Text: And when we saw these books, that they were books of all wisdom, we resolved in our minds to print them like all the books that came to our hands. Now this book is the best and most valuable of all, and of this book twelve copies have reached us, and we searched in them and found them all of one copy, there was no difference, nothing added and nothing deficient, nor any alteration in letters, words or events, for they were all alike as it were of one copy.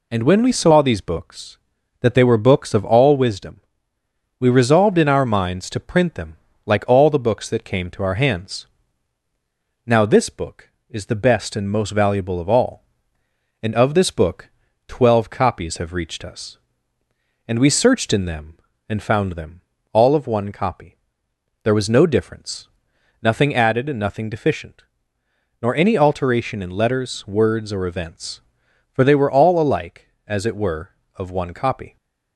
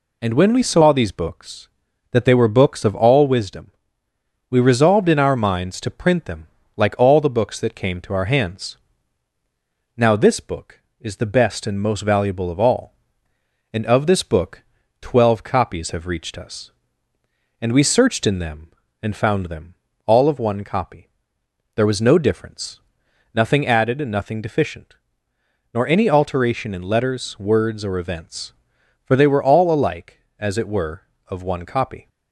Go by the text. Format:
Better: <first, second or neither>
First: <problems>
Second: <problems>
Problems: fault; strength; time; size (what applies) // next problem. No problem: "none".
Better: neither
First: pauses between "them" and "like"; slight; at 6.3 s; 0.28 s long // pauses between "book" and "twelve"; at 14.5 s; 0.38 s long // pauses between "them" and "all"; slight; at 19.6 s; 0.30 s long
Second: pauses between "them" and "like"; slight; at 6.4 s; 0.28 s long // pauses between "book" and "twelve"; at 14.6 s; 0.38 s long // pauses between "them" and "all"; slight; at 19.7 s; 0.30 s long